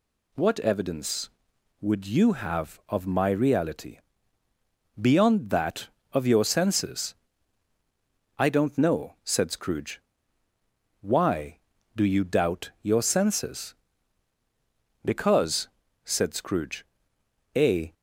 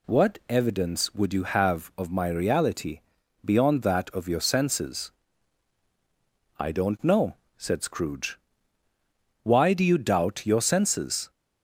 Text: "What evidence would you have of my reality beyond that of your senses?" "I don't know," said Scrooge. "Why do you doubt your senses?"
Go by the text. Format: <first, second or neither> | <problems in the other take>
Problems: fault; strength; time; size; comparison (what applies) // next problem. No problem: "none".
second | pauses between "reality" and "beyond"; at 3.9 s; 1.0 s long; also in the second // goes on to say "Because said Scrooge a"; strong; from 15.0 s on; 2.9 s long